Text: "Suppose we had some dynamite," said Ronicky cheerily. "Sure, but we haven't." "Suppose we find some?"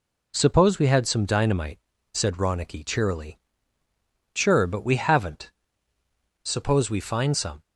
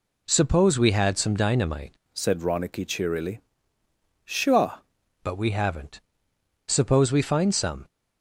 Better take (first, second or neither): first